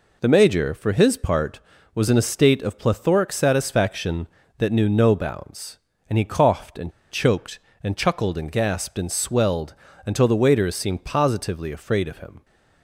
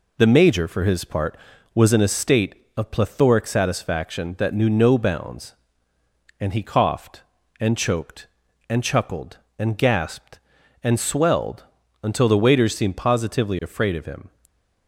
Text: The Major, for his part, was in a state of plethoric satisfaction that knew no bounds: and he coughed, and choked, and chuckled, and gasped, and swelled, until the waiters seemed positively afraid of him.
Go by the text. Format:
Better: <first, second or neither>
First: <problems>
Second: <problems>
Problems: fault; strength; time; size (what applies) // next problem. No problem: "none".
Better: second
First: pauses between "and" and "choked"; slight; at 6.9 s; 0.20 s long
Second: none